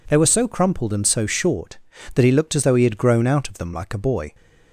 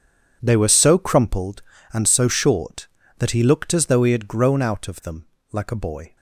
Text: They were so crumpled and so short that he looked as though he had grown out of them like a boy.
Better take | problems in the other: first | gets quieter; strong; throughout; 16 dB // pauses between "them" and "like"; slight; at 5.2 s; 0.26 s long

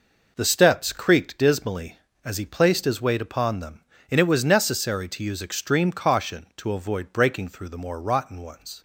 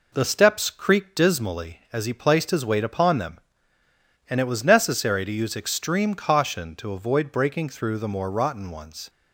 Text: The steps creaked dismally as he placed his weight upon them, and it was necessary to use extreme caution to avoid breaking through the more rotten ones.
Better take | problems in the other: neither | none

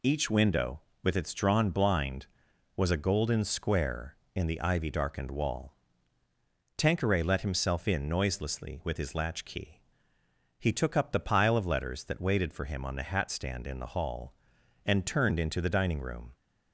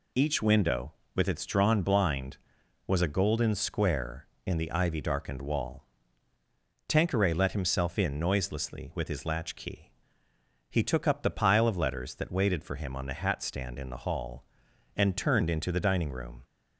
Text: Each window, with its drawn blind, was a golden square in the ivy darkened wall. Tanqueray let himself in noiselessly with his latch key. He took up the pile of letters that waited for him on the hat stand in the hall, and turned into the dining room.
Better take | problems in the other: neither | none

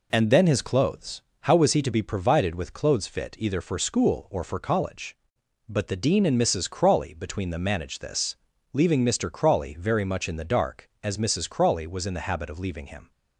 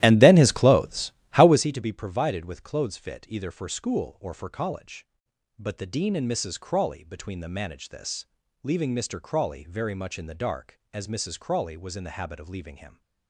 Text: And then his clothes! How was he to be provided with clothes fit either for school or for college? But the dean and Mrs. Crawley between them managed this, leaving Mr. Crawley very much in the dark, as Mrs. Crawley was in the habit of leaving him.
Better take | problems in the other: first | starts louder than the rest; strong; until 1.7 s; 14 dB

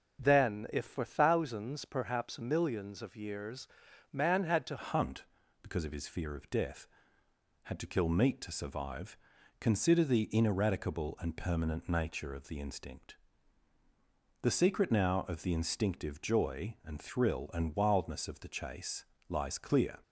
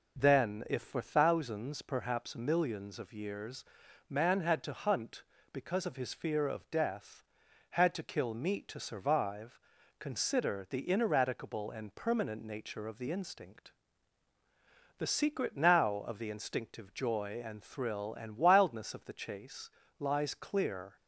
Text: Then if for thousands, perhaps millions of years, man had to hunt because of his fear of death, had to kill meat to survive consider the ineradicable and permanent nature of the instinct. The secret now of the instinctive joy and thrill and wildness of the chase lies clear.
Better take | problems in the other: second | starts louder than the rest; until 1.2 s; 7 dB // changes voice at "hunt"; from 4.7 s on; 15.2 s long // pauses between "survive" and "consider"; at 9.1 s; 0.44 s long; also in the second // pauses between "chase" and "lies"; slight; at 19.0 s; 0.24 s long; slight in the second

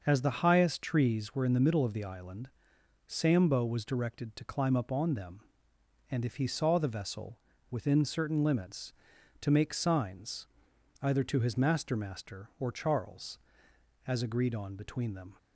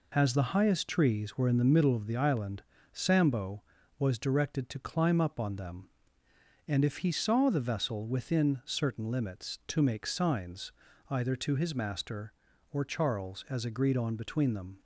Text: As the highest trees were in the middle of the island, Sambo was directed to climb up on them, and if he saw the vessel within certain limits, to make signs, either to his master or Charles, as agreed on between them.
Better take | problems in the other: second | starts louder than the rest; noticeable; until 1.0 s; 6 dB // pauses between "vessel" and "within"; slight; at 7.3 s; 0.32 s long // says "master" twice; at 11.9 s

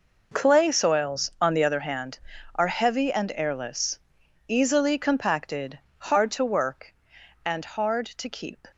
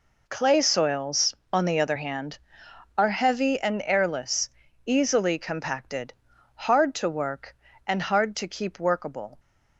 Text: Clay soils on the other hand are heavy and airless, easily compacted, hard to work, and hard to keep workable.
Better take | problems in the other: second | stops before "workable"; at 8.7 s

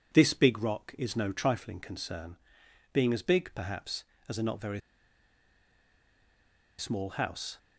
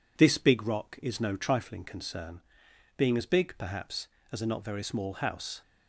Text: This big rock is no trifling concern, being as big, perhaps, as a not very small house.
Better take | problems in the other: second | pauses between "very" and "small"; strong; at 4.7 s; 1.9 s long

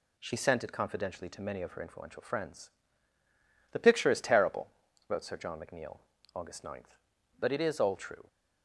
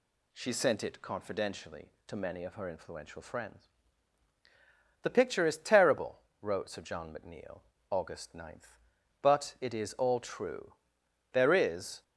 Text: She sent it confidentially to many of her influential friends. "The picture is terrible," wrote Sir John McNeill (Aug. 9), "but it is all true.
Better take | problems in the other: first | goes on to say "There is"; noticeable; from 11.3 s on; 0.70 s long

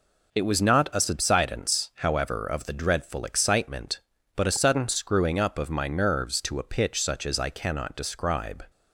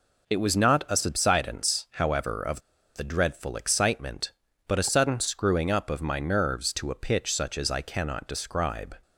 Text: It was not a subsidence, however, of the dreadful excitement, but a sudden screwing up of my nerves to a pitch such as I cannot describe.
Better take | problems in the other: first | pauses between "of" and "the"; slight; at 2.6 s; 0.34 s long

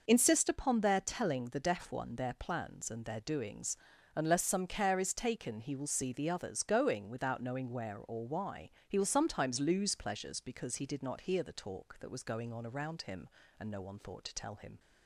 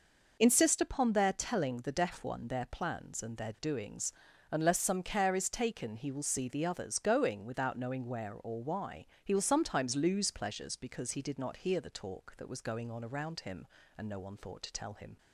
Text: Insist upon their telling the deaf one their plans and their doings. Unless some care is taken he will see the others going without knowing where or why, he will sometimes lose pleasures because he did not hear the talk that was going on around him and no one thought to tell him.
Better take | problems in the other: neither | none

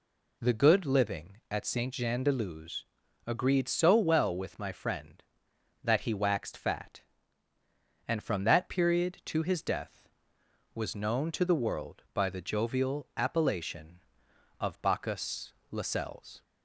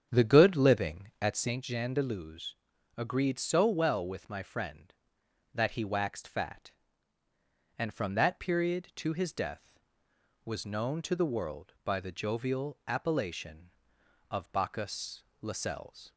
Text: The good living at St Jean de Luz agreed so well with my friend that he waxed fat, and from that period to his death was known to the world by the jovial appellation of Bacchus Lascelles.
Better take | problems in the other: first | starts louder than the rest; strong; until 1.6 s; 8 dB // pauses between "Luz" and "agreed"; at 2.5 s; 0.42 s long; also in the first // pauses between "Bacchus" and "Lascelles"; slight; at 15.2 s; 0.16 s long; slight in the first

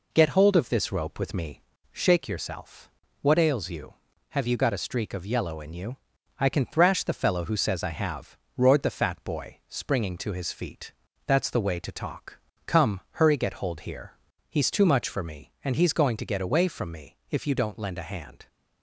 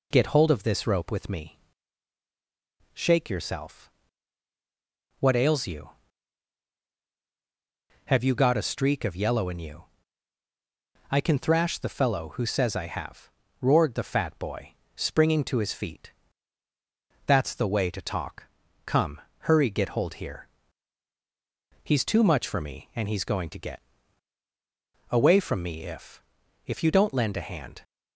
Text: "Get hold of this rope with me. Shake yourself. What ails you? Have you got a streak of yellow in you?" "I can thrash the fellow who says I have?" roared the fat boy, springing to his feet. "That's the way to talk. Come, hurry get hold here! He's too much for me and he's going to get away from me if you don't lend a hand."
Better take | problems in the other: first | pauses between "get" and "away"; strong; at 23.8 s; 1.2 s long // says "if" twice; at 26.6 s

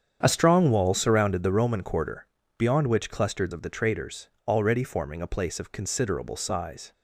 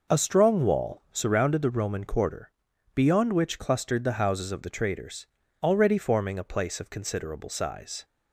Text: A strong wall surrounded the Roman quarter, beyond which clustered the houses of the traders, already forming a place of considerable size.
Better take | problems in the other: second | starts louder than the rest; strong; until 1.2 s; 8 dB // skips "the houses"; at 3.5 s

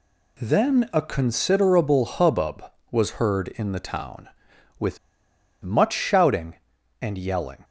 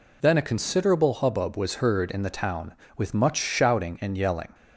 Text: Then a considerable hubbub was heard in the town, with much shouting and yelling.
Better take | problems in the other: second | pauses between "with" and "much"; noticeable; at 4.9 s; 0.66 s long

